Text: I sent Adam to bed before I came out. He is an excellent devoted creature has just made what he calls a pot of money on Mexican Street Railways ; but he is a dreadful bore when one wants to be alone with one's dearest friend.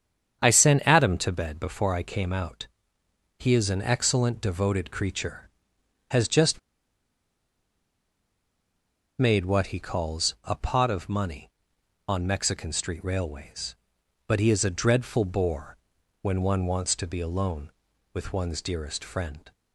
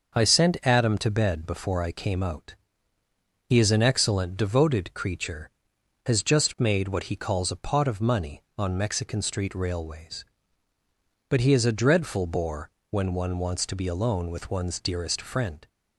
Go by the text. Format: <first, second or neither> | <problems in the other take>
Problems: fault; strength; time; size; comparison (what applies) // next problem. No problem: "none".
second | starts louder than the rest; strong; until 1.4 s; 8 dB; also in the second // pauses between "just" and "made"; strong; at 6.5 s; 2.5 s long // pauses between "bore" and "when"; at 15.7 s; 0.44 s long; slight in the second